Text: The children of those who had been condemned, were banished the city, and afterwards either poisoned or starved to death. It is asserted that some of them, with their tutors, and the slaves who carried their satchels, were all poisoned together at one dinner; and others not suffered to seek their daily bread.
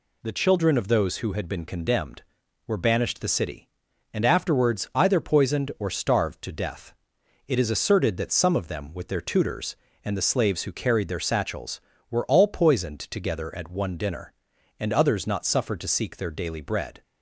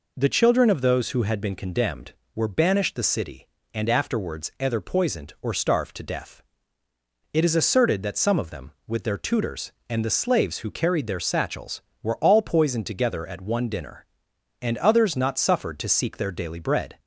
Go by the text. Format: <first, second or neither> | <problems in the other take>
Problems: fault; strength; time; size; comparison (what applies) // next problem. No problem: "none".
neither | none